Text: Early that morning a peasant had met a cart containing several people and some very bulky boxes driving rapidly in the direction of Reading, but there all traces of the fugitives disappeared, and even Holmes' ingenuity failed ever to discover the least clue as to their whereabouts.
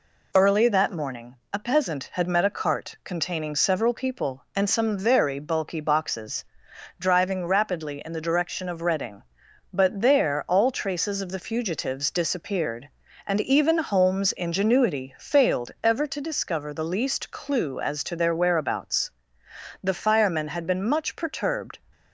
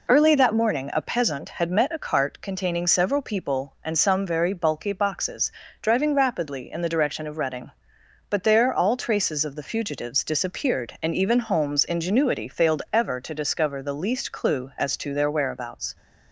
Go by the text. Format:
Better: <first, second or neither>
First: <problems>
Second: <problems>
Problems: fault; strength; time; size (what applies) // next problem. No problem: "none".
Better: second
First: pauses between "morning" and "a"; slight; at 1.3 s; 0.16 s long // pauses between "boxes" and "driving"; noticeable; at 6.4 s; 0.52 s long // goes on to say "The firemen had been much perturbed"; strong; from 19.8 s on; 1.9 s long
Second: pauses between "boxes" and "driving"; slight; at 5.5 s; 0.30 s long